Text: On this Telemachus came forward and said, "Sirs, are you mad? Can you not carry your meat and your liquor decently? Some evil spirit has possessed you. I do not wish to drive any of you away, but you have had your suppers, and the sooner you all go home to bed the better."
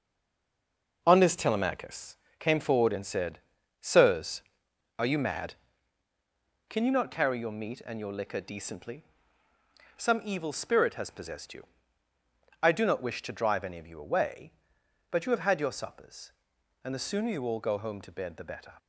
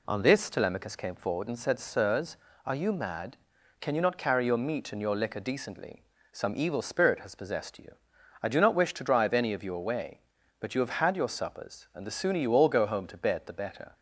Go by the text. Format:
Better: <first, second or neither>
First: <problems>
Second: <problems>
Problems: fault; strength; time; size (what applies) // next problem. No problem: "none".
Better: second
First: stays silent before the first word; until 1.0 s; 1.0 s long // pauses between "Telemachus" and "came"; slight; at 2.1 s; 0.22 s long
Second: none